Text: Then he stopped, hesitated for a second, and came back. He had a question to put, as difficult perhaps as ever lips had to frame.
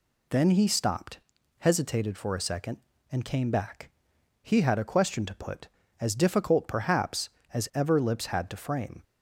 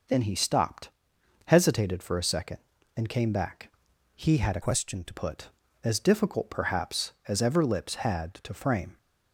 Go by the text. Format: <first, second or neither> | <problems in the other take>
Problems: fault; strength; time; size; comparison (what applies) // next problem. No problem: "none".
first | changes voice from "question" to "to"; from 4.6 to 5.1 s; 0.5 s long